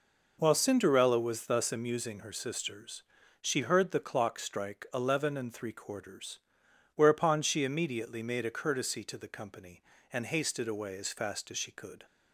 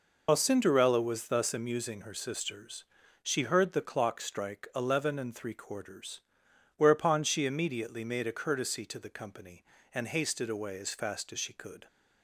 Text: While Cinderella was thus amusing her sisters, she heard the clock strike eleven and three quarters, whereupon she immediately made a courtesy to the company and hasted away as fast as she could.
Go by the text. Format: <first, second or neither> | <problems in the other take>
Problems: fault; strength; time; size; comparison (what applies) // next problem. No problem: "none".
first | loses the start of "While"; at 0.2 s; 80 ms